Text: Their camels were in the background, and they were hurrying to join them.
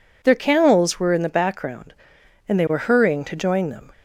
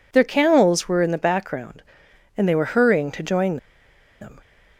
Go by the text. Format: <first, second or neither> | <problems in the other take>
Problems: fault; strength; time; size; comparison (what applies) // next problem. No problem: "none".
first | pauses between "join" and "them"; noticeable; at 3.5 s; 0.64 s long